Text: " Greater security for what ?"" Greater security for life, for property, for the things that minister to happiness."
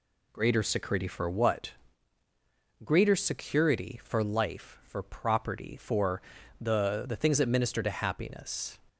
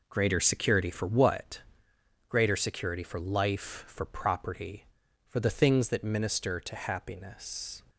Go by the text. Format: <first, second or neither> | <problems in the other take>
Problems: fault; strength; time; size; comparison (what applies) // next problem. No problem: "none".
second | pauses between "for" and "the"; at 6.2 s; 0.40 s long // says "the" twice; at 7.0 s